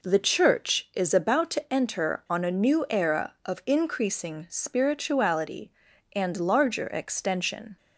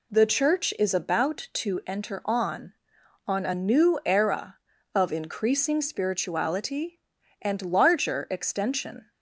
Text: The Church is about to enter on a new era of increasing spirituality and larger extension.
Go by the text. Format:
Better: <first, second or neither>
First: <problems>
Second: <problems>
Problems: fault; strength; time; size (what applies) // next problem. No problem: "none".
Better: first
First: none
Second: says "on" twice; at 3.2 s